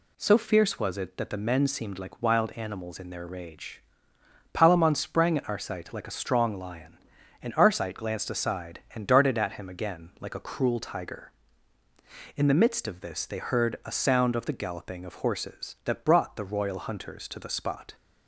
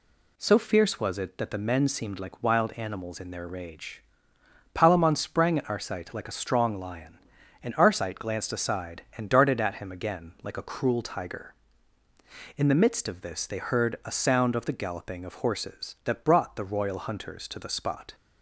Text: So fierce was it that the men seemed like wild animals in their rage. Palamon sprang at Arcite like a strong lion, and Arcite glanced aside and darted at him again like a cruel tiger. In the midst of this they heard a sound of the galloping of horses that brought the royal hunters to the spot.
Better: neither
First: none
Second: none

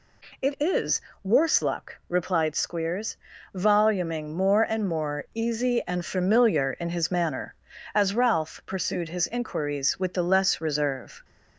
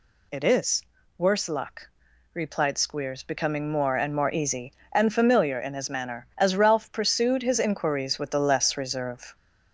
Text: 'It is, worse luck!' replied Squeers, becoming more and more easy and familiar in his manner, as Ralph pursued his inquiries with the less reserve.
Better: second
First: says "voluming" for "becoming"; at 3.5 s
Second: none

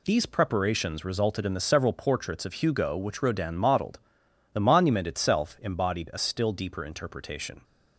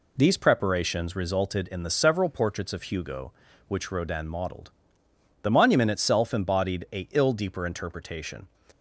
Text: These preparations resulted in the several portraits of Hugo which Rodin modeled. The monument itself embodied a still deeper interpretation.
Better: first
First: none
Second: says "ill" for "still"; at 7.1 s

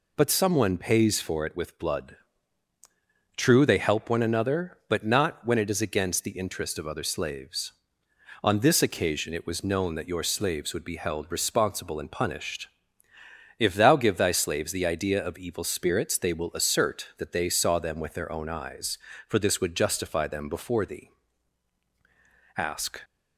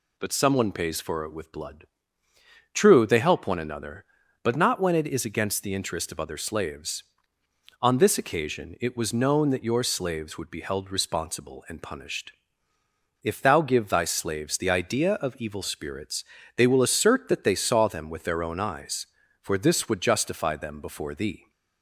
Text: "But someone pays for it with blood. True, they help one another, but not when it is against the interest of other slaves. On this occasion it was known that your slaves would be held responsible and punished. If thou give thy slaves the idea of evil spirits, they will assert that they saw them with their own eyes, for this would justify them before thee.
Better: second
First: goes on to say "Ask"; slight; from 22.5 s on; 0.46 s long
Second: none

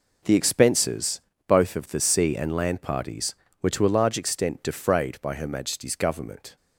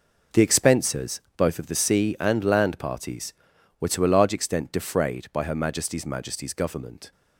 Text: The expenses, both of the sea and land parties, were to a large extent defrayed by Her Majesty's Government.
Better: first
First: none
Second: says "Majesty's" twice; at 6.0 s

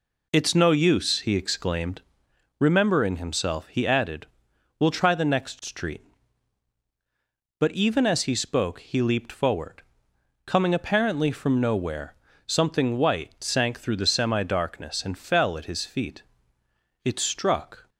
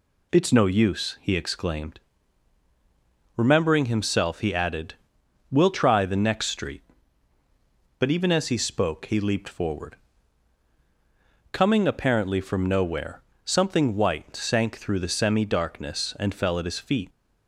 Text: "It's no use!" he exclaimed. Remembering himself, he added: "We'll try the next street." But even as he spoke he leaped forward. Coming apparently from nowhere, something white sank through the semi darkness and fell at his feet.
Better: second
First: goes on to say "It struck"; noticeable; from 17.0 s on; 0.86 s long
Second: none

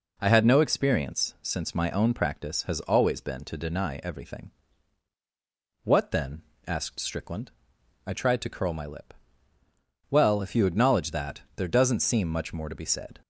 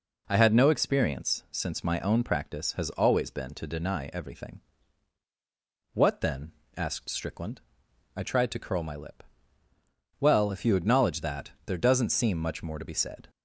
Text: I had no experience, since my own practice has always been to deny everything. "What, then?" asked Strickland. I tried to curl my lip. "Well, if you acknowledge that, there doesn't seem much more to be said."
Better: neither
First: none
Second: none

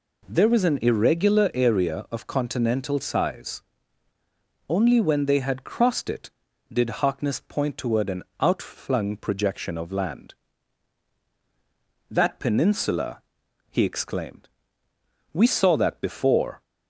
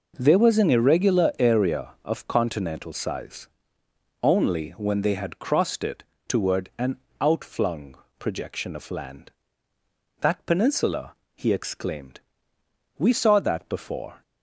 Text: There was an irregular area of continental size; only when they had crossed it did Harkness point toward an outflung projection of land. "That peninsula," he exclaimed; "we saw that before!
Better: first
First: pauses between "an" and "outflung"; slight; at 8.2 s; 0.18 s long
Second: skips "did Harkness point"; at 6.1 s // pauses between "an" and "outflung"; slight; at 6.9 s; 0.22 s long // pauses between "outflung" and "projection"; slight; at 7.9 s; 0.22 s long

